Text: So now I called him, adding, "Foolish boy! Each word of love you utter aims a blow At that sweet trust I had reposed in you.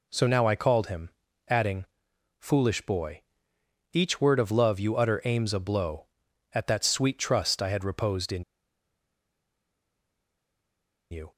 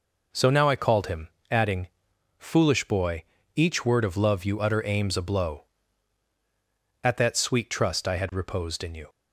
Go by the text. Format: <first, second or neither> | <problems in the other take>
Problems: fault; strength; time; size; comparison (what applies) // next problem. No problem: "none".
second | pauses between "in" and "you"; strong; at 8.4 s; 2.6 s long